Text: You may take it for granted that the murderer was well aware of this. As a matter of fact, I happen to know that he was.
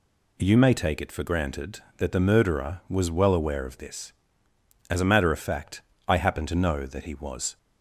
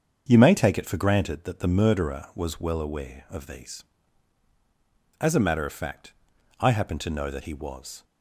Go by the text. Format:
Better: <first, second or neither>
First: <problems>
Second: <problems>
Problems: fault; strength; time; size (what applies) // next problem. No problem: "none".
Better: first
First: none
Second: starts louder than the rest; until 1.3 s; 7 dB // says "these" for "this"; at 3.4 s